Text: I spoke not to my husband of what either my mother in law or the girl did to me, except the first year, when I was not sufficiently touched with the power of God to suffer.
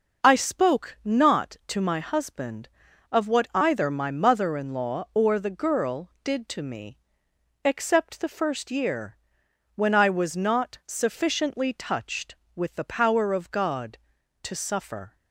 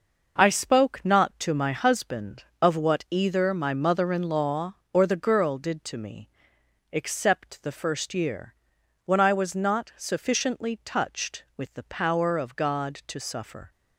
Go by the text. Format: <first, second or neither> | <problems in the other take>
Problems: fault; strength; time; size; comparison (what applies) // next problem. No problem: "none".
neither | none